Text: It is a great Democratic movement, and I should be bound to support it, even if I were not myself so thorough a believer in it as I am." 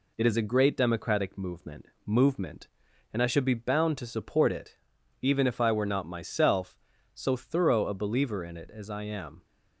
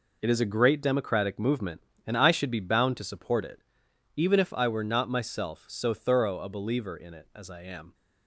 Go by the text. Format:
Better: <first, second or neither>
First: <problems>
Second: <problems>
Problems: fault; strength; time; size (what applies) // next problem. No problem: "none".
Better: second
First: says "movement" twice; at 2.0 s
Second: none